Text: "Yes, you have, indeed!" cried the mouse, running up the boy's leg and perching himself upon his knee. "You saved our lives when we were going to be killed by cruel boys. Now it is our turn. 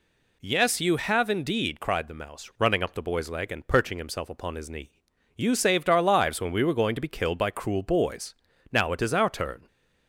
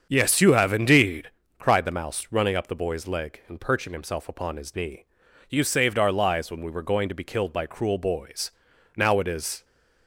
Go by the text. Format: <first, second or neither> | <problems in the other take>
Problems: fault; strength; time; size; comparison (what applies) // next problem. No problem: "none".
first | starts louder than the rest; strong; until 1.1 s; 7 dB // stops before "our turn"; at 9.6 s